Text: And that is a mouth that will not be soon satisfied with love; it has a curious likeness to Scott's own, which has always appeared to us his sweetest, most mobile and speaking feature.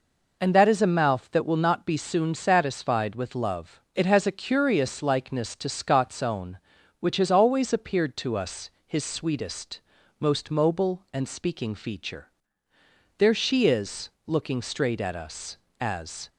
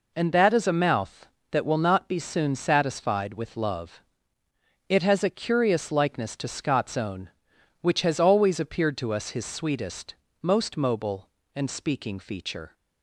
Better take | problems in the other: second | pauses between "us" and "his"; slight; at 8.6 s; 0.18 s long // goes on to say "There she is looking straight at us as"; strong; from 13.1 s on; 3.1 s long

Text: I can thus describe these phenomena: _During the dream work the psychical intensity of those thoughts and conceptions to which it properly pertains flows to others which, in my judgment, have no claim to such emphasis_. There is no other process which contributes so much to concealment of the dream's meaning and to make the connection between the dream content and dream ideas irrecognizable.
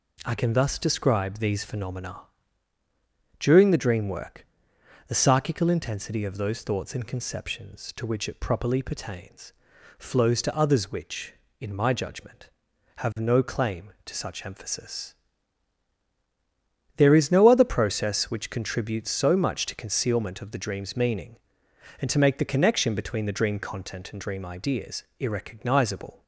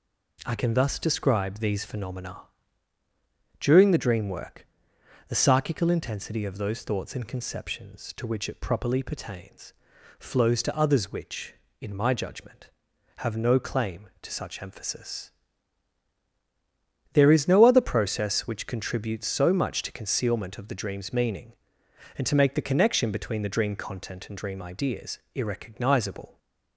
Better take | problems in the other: neither | pauses between "work" and "the"; noticeable; the same in both // pauses between "pertains" and "flows"; the same in both // pauses between "ideas" and "irrecognizable"; slight; the same in both

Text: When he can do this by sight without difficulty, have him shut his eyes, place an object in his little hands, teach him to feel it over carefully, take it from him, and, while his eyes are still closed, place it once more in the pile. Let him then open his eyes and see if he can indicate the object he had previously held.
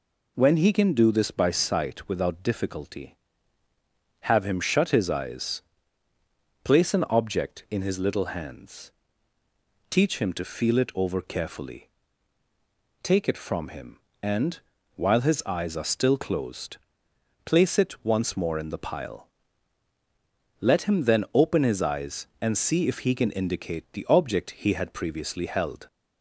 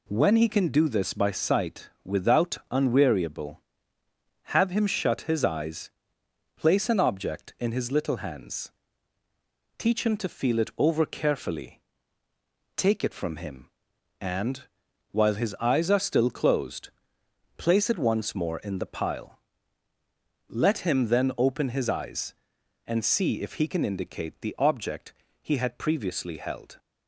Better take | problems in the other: first | pauses between "sight" and "without"; slight; at 1.8 s; 0.16 s long // says "unweariable" for "difficulty"; at 2.7 s // pauses between "object" and "he"; slight; at 25.1 s; 0.30 s long

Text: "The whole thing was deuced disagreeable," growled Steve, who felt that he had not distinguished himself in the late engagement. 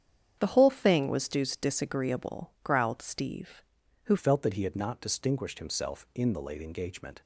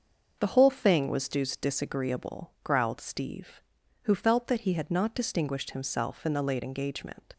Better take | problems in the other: second | starts louder than the rest; strong; until 1.4 s; 8.5 dB; also in the second // changes voice at "felt"; from 4.1 s on; 3.1 s long

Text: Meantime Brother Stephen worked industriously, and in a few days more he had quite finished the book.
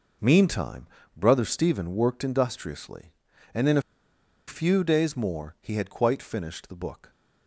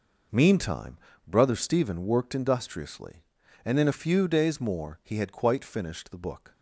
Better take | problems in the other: second | pauses between "Meantime" and "Brother"; slight; at 0.8 s; 0.30 s long; slight in the second // pauses between "a" and "few"; noticeable; at 3.8 s; 0.66 s long

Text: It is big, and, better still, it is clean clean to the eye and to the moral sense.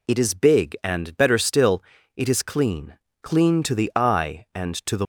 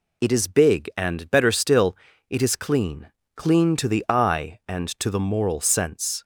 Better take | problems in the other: second | pauses between "clean" and "clean"; slight; at 2.9 s; 0.26 s long; slight in the second // stops before "moral sense"; at 5.0 s

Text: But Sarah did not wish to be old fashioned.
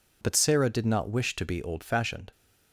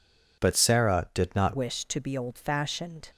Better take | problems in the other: first | changes voice at "wish"; from 1.5 s on; 1.5 s long

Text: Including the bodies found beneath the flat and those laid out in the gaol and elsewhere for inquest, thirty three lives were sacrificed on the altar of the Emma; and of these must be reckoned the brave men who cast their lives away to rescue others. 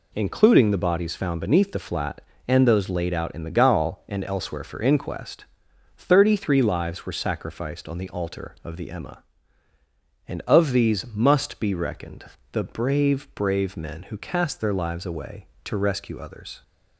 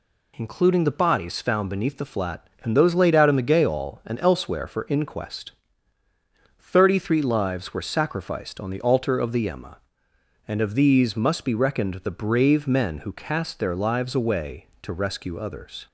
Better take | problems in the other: second | pauses between "reckoned" and "the"; slight; at 12.2 s; 0.26 s long // says "brave" twice; at 13.3 s

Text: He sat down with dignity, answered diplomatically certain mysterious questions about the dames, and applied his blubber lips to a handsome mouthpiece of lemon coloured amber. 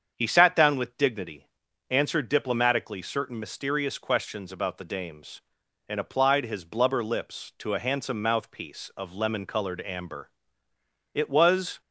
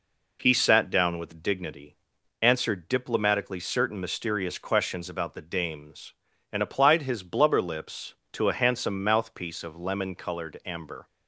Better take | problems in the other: second | starts louder than the rest; strong; until 1.1 s; 7.5 dB // goes on to say "It was"; noticeable; from 11.1 s on; 0.68 s long

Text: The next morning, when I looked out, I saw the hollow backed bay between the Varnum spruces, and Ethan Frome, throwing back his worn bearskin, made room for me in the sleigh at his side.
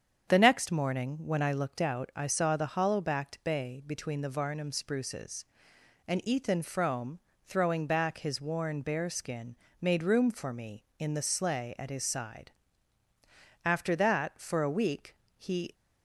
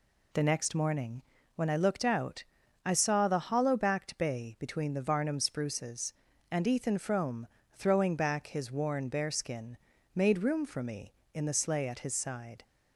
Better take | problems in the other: second | starts louder than the rest; strong; until 1.3 s; 7.5 dB // goes on to say "After that for a week he"; strong; from 13.6 s on; 2.1 s long

